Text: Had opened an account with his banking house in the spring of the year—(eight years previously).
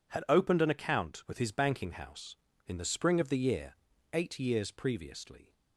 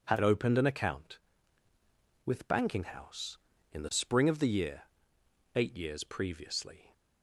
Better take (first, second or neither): first